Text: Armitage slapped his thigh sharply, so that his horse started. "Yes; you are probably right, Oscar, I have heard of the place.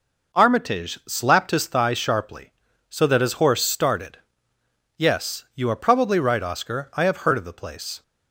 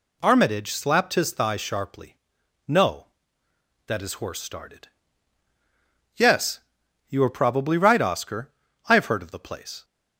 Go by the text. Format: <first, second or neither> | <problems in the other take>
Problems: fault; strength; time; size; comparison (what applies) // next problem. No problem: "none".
first | says "no" for "so"; at 2.6 s